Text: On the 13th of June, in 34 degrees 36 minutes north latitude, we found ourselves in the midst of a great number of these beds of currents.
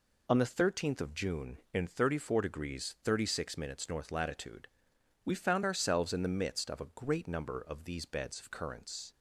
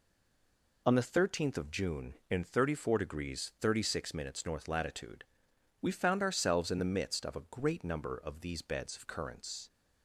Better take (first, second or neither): first